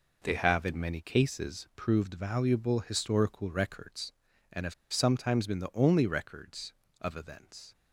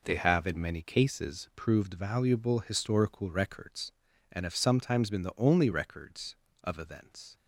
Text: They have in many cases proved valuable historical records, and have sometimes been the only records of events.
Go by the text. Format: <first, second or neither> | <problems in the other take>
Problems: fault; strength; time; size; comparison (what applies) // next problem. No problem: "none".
second | pauses between "have" and "sometimes"; slight; at 4.7 s; 0.19 s long